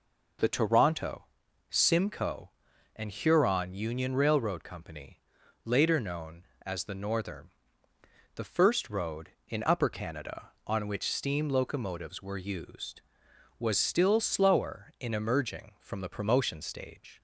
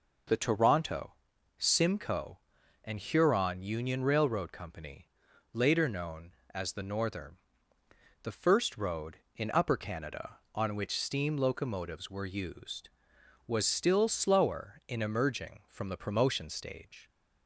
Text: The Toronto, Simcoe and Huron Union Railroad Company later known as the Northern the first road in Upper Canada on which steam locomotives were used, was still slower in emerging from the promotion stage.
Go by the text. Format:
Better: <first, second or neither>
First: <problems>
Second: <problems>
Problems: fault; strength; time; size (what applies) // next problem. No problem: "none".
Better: neither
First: pauses between "Company" and "later"; noticeable; at 5.1 s; 0.46 s long // pauses between "Northern" and "the"; noticeable; at 7.4 s; 0.86 s long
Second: pauses between "Company" and "later"; noticeable; at 5.0 s; 0.46 s long // pauses between "Northern" and "the"; noticeable; at 7.3 s; 0.86 s long